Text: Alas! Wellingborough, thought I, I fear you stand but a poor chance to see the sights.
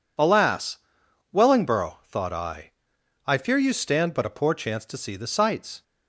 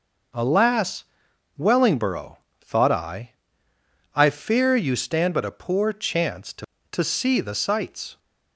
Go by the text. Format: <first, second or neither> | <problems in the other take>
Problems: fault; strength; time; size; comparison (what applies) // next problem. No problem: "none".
first | says "to" twice; at 6.9 s